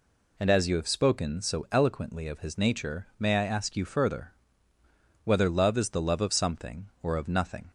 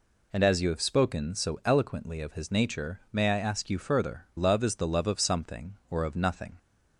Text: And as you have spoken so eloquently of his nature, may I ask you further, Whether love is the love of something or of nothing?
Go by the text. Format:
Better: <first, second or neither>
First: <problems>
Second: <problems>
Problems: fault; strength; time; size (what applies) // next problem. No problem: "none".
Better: first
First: none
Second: skips "Whether"; at 4.3 s